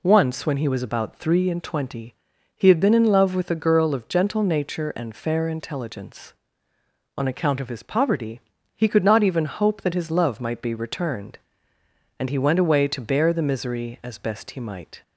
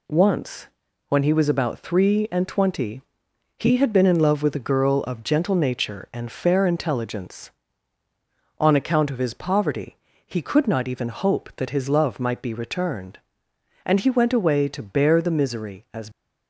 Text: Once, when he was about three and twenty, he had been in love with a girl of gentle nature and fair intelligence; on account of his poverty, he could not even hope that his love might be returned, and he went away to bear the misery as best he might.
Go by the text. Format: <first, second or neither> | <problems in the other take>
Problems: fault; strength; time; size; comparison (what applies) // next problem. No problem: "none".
first | stops before "best he might"; at 16.1 s